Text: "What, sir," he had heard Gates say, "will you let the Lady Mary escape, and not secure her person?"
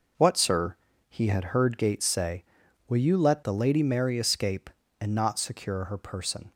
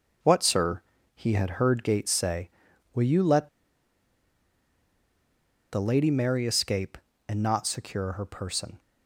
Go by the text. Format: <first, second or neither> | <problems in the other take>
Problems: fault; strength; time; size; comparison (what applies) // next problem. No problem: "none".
first | pauses between "let" and "the"; strong; at 3.4 s; 2.2 s long